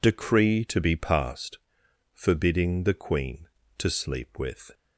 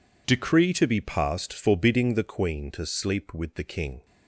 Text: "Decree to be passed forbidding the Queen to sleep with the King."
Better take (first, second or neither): second